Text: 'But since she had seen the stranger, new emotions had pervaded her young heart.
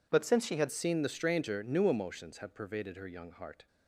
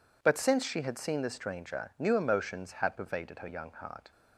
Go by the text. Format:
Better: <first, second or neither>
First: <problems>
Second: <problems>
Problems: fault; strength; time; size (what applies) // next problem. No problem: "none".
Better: second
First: changes voice at "seen"; from 0.7 s on; 2.9 s long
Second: none